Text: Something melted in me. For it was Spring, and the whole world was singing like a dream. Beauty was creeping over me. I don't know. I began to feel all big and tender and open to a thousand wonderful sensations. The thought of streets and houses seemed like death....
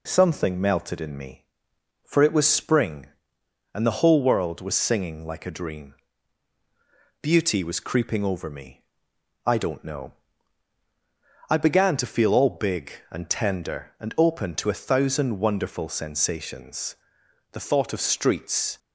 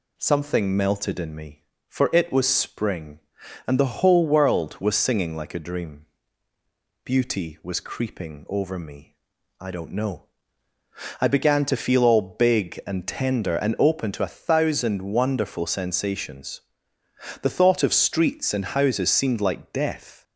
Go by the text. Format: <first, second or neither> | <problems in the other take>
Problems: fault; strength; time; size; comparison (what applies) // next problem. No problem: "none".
second | stops before "and houses seemed like death"; at 18.7 s